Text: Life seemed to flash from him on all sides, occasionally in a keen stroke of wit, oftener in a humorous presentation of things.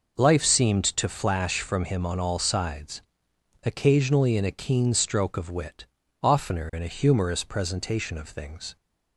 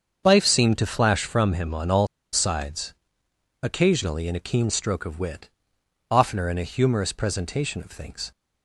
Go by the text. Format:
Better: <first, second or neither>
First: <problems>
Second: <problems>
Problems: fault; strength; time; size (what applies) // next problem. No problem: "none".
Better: first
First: none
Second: starts louder than the rest; until 1.2 s; 7 dB // pauses between "all" and "sides"; slight; at 2.0 s; 0.27 s long